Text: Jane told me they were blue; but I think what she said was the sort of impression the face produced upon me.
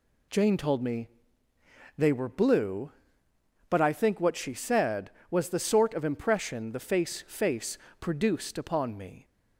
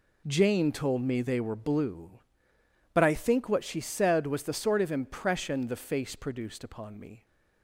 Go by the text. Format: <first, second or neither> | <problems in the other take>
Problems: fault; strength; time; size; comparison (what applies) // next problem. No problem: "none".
second | pauses between "me" and "they"; noticeable; at 1.0 s; 0.90 s long // says "face" twice; at 7.2 s